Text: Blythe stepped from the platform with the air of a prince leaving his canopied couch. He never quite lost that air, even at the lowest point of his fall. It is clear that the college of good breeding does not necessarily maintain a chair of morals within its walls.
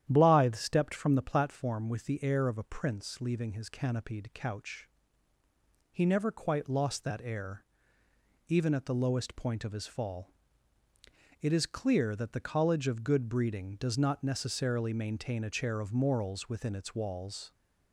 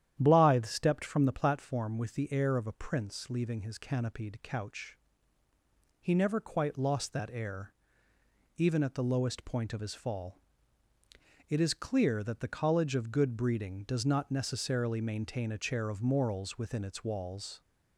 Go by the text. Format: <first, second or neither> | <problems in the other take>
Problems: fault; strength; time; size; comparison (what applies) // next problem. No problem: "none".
neither | starts louder than the rest; strong; the same in both